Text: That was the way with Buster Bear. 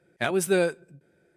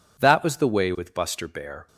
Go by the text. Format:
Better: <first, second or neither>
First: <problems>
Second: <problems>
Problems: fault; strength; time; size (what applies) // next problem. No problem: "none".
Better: second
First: stops before "way with Buster Bear"; at 0.9 s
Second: none